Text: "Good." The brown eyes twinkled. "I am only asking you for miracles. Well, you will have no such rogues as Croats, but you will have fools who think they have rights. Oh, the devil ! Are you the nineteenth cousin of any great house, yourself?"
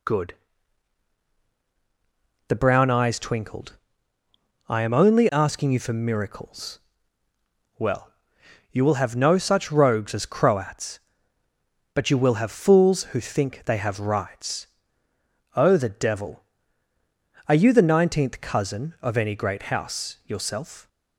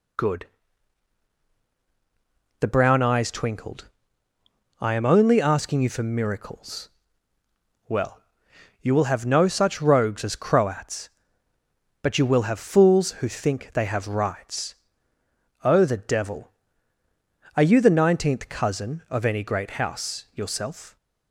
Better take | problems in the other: neither | none

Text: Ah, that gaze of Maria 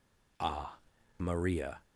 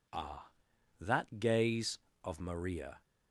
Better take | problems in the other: second | skips "that gaze of"; at 0.9 s

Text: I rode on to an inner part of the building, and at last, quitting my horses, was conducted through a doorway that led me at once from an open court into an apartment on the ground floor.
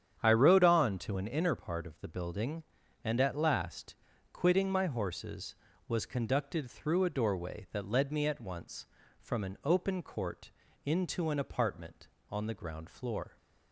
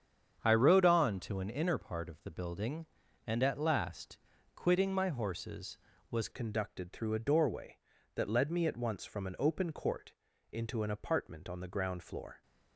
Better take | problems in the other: first | starts louder than the rest; strong; until 1.4 s; 8 dB; strong in the first // changes voice at "conducted"; from 6.3 s on; 6.1 s long // pauses between "court" and "into"; slight; at 10.1 s; 0.36 s long; slight in the first

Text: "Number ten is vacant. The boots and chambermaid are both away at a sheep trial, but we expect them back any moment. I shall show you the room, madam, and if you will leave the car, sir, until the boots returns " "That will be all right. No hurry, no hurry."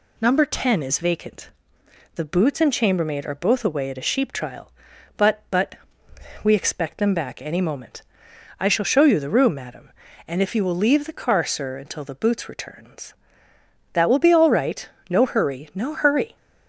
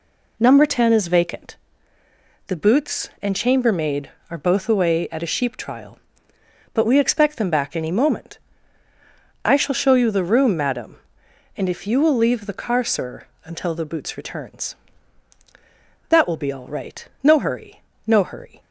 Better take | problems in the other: second | says "but" twice; at 5.5 s

